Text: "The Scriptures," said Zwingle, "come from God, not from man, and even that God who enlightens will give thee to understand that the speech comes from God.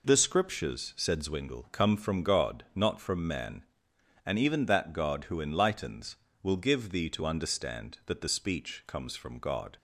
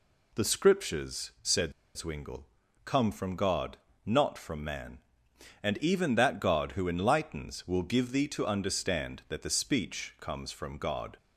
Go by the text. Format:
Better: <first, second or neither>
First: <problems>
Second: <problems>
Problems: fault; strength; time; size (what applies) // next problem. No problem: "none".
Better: first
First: none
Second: pauses between "said" and "Zwingle"; slight; at 1.7 s; 0.24 s long